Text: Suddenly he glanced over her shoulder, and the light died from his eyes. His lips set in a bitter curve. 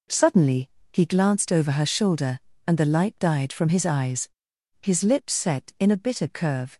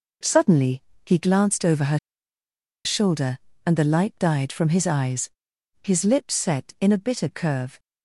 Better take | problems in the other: first | pauses between "Suddenly" and "he"; slight; at 0.8 s; 0.20 s long; slight in the first // pauses between "her" and "shoulder"; noticeable; at 1.9 s; 0.86 s long

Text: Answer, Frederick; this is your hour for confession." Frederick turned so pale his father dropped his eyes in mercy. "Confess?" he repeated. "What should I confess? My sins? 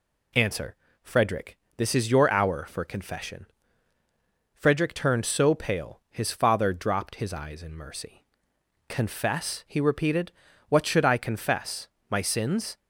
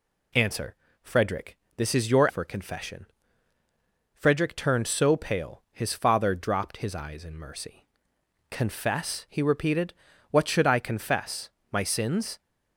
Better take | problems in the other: first | skips "hour"; at 2.2 s

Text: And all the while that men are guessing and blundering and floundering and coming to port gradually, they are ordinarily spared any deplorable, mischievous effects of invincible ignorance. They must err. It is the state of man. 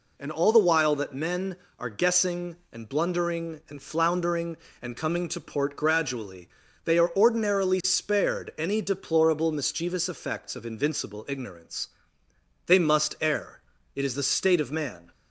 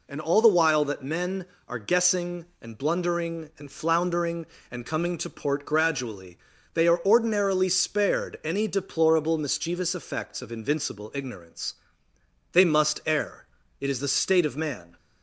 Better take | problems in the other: neither | none

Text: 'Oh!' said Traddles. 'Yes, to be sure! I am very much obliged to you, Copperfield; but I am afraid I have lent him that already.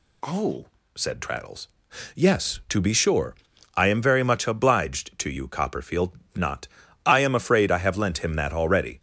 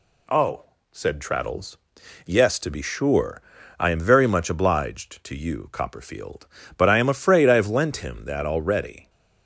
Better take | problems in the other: second | says "not" for "but"; at 6.3 s

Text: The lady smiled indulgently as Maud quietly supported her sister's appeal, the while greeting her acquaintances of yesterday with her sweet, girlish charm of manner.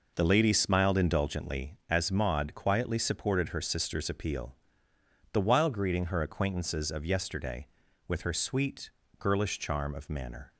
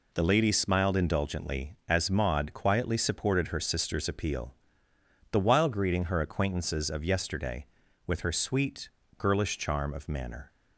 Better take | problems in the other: second | starts louder than the rest; noticeable; until 1.6 s; 5 dB

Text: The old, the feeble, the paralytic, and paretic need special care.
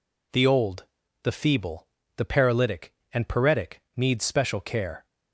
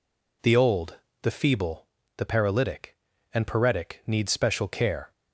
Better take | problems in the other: neither | none

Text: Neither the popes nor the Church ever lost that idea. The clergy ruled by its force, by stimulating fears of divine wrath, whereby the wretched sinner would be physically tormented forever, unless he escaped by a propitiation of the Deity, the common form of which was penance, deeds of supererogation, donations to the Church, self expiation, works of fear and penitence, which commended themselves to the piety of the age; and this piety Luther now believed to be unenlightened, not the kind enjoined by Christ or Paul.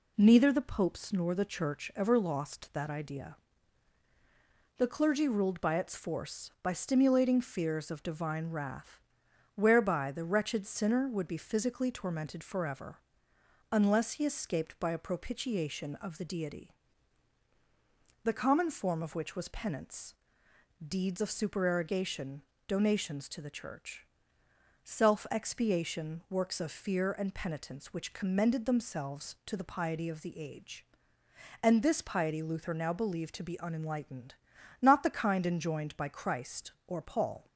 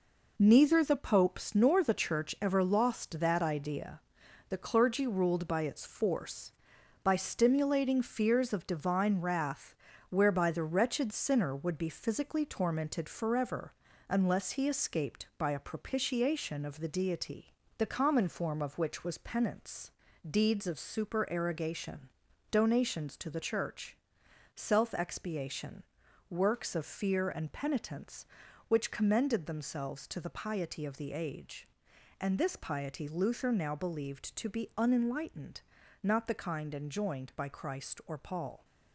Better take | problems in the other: first | gets quieter; throughout; 7 dB

